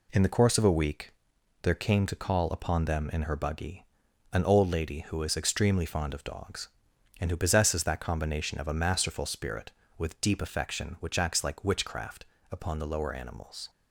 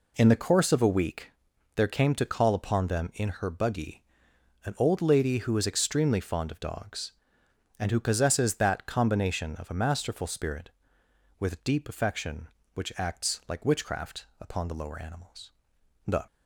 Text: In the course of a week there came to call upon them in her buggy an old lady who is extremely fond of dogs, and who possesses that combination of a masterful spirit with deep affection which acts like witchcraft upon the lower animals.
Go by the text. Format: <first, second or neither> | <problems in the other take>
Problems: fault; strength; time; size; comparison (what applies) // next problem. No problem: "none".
first | pauses between "week" and "there"; at 1.3 s; 0.44 s long; noticeable in the first // pauses between "buggy" and "an"; noticeable; at 4.0 s; 0.62 s long; noticeable in the first // pauses between "witchcraft" and "upon"; slight; at 14.2 s; 0.16 s long; slight in the first // goes on to say "The"; slight; from 16.0 s on; 0.18 s long